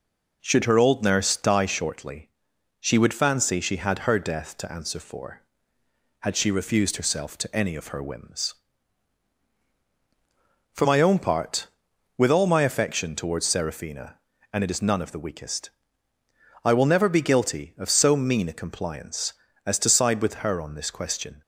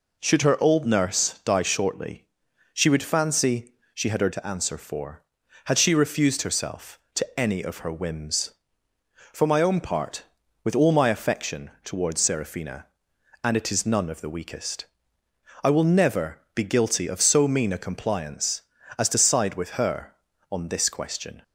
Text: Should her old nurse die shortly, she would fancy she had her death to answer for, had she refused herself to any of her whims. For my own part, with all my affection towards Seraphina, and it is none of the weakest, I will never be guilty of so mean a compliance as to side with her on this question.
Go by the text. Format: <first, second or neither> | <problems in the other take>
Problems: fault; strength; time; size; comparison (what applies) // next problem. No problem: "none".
first | pauses between "fancy" and "she"; slight; at 3.7 s; 0.22 s long // skips "death"; at 4.3 s // pauses between "never" and "be"; slight; at 16.4 s; 0.16 s long